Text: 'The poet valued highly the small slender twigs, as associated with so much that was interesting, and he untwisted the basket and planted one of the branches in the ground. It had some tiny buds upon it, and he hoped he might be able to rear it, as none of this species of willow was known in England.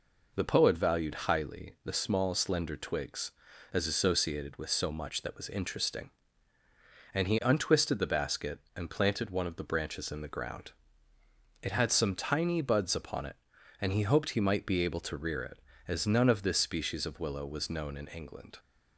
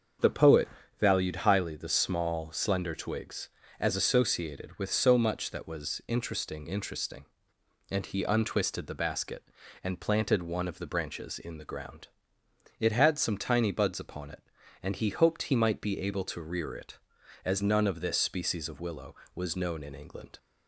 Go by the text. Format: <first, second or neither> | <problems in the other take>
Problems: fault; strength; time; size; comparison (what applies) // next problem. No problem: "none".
first | starts louder than the rest; strong; until 1.5 s; 7.5 dB // pauses between "poet" and "valued"; slight; at 0.6 s; 0.32 s long // says "interesting" twice; at 6.6 s